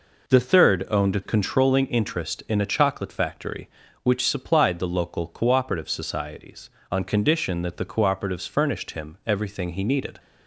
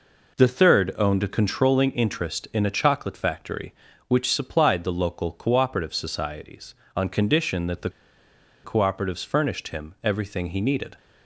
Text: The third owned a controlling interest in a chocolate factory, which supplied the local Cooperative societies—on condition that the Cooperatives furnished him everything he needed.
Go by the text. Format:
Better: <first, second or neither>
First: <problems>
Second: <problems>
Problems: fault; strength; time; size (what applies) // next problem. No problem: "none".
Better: first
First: none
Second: pauses between "the" and "Cooperatives"; noticeable; at 7.8 s; 0.74 s long